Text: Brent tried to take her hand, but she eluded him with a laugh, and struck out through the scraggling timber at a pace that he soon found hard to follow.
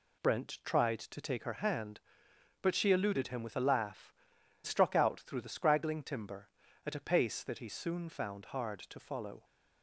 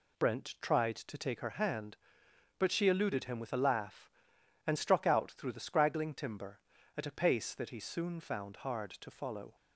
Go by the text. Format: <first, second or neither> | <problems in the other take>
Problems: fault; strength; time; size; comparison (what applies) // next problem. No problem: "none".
second | skips "and"; at 4.3 s